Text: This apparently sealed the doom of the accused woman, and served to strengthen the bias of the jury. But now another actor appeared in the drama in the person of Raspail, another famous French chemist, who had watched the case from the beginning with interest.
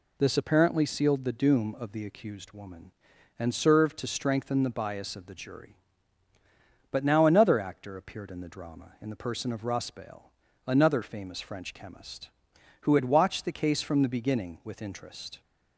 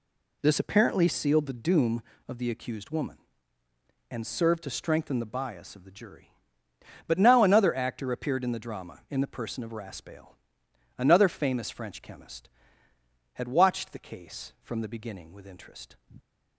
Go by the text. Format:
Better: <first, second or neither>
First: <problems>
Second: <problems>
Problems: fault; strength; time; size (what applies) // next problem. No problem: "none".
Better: first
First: none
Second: skips "who"; at 12.9 s